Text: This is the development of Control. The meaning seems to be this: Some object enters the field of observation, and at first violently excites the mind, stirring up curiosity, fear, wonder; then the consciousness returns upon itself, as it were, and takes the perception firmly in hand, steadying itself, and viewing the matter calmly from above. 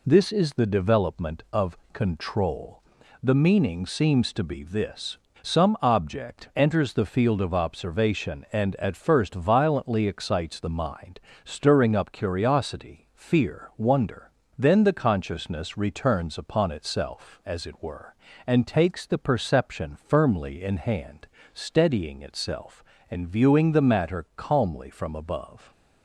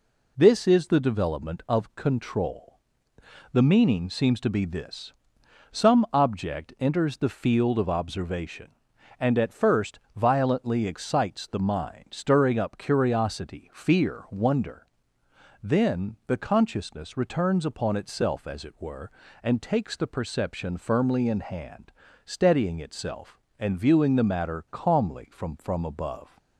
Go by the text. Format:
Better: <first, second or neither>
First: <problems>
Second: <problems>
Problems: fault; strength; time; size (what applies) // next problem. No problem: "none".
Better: first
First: none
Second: pauses between "first" and "violently"; slight; at 10.0 s; 0.16 s long // says "from" twice; at 25.5 s